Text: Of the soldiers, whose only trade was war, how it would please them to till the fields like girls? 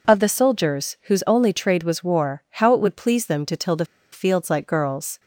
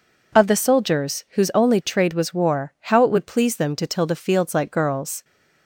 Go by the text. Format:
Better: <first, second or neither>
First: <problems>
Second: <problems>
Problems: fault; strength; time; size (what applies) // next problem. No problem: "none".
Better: second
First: pauses between "the" and "fields"; slight; at 3.8 s; 0.28 s long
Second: none